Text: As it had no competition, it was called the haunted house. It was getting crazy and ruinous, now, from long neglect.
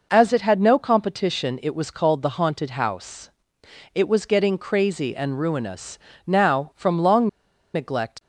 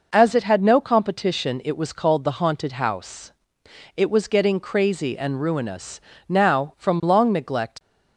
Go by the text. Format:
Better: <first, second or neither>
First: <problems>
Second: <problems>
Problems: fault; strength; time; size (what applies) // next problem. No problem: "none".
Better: second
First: pauses between "long" and "neglect"; noticeable; at 7.2 s; 0.47 s long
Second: none